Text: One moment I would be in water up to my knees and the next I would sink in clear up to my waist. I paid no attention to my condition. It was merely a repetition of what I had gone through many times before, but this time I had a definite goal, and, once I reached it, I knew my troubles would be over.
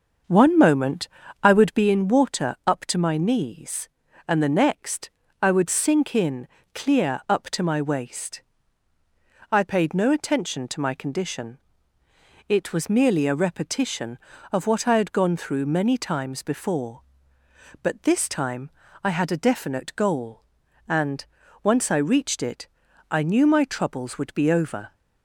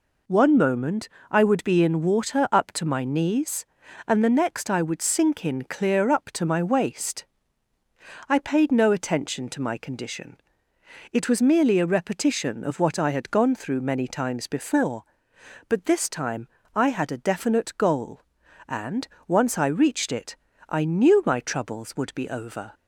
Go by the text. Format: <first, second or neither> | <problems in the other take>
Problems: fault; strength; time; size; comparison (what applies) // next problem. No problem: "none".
second | starts louder than the rest; until 1.9 s; 6.5 dB // pauses between "moment" and "I"; slight; at 1.0 s; 0.34 s long; slight in the second // pauses between "next" and "I"; slight; at 5.1 s; 0.32 s long // pauses between "in" and "clear"; slight; at 6.4 s; 0.26 s long // pauses between "time" and "I"; slight; at 18.7 s; 0.34 s long; slight in the second